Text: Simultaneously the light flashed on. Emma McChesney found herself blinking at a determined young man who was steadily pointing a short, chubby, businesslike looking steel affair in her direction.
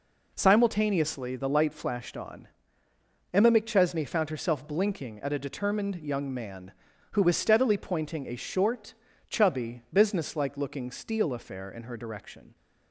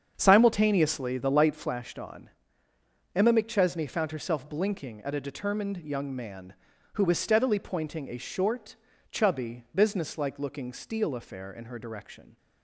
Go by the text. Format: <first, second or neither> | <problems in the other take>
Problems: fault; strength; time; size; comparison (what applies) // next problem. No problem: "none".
first | starts louder than the rest; strong; until 1.8 s; 7.5 dB